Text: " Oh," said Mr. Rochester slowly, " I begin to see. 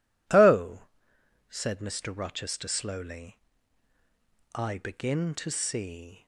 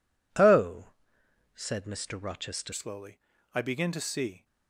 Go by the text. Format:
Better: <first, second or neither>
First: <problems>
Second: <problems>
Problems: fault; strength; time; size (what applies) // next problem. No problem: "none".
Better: first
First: none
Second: changes voice at "slowly"; from 2.7 s on; 1.7 s long